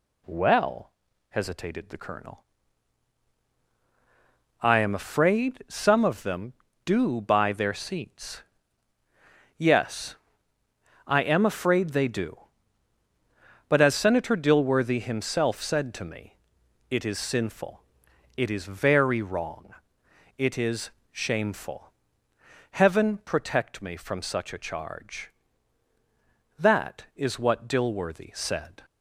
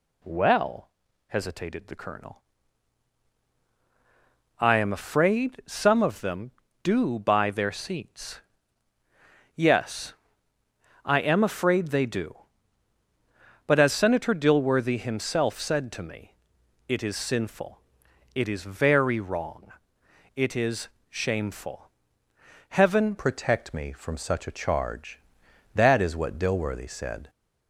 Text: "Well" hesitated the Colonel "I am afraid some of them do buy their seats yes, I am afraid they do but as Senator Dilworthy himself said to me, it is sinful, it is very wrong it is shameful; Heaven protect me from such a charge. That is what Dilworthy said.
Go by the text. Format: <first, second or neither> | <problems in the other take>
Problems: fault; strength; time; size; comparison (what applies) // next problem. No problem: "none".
first | pauses between "Well" and "hesitated"; at 0.8 s; 0.40 s long; also in the first // pauses between "Colonel" and "I"; strong; at 2.4 s; 2.1 s long; strong in the first // pauses between "seats" and "yes"; at 8.3 s; 1.1 s long; also in the first // pauses between "wrong" and "it"; noticeable; at 19.7 s; 0.64 s long; noticeable in the first // pauses between "is" and "shameful"; slight; at 20.8 s; 0.22 s long; slight in the first // changes voice at "protect"; from 23.1 s on; 4.1 s long